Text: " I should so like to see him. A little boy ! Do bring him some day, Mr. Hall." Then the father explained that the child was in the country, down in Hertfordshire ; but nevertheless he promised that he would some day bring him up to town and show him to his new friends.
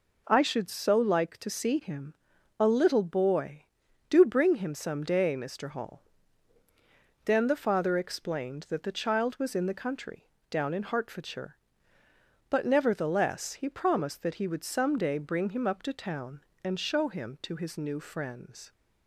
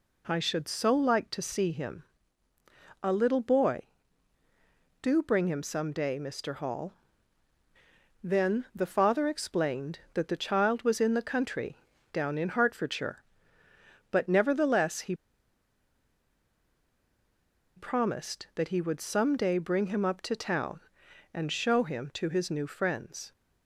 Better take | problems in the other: first | pauses between "he" and "promised"; strong; at 15.1 s; 2.6 s long

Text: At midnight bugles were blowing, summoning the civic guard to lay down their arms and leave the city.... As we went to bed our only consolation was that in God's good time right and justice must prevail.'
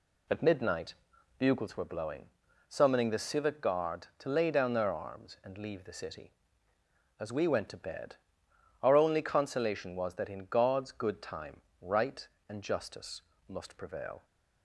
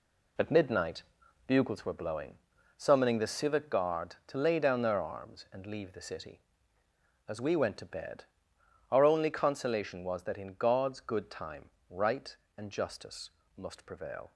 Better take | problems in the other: first | gets quieter; strong; throughout; 8 dB // pauses between "midnight" and "bugles"; at 1.0 s; 0.42 s long; also in the first // pauses between "bed" and "our"; noticeable; at 8.2 s; 0.66 s long; noticeable in the first // pauses between "time" and "right"; slight; at 11.6 s; 0.20 s long; slight in the first // pauses between "justice" and "must"; slight; at 13.2 s; 0.26 s long; slight in the first

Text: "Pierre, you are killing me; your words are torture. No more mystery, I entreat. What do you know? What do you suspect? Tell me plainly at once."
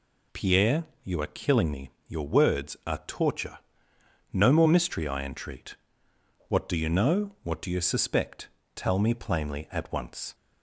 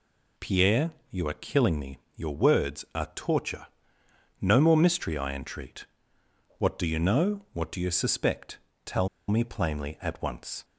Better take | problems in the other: first | pauses between "Tell" and "me"; slight; at 9.0 s; 0.19 s long

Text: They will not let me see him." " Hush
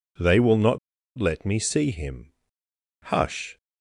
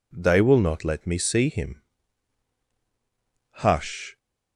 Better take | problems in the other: second | pauses between "not" and "let"; at 0.7 s; 0.40 s long

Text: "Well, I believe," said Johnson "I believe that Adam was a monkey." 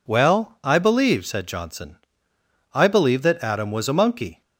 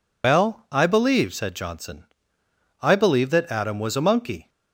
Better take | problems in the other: first | loses the start of "Well"; at 0.2 s; 95 ms // pauses between "Johnson" and "I"; noticeable; at 2.0 s; 0.76 s long; noticeable in the first

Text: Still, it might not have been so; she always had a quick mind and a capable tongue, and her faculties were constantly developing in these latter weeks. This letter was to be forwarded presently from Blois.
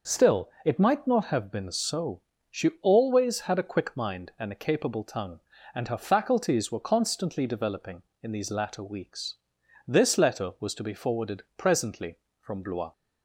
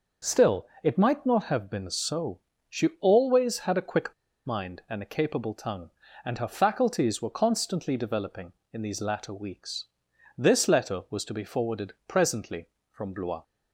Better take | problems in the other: first | starts louder than the rest; noticeable; until 1.4 s; 6 dB // pauses between "quick" and "mind"; slight; at 4.1 s; 0.32 s long // pauses between "forwarded" and "presently"; slight; at 11.9 s; 0.16 s long; slight in the first

